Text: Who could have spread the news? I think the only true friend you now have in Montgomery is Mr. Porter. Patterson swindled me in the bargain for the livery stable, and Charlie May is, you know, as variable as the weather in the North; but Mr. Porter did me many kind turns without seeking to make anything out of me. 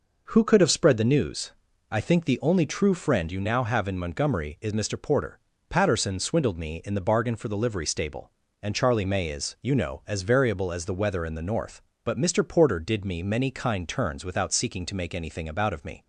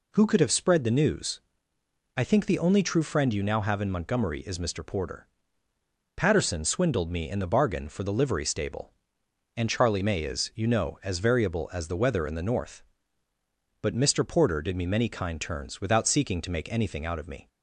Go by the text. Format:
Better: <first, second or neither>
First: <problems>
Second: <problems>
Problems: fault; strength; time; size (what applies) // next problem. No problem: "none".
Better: second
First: says "about" for "out"; at 15.4 s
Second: none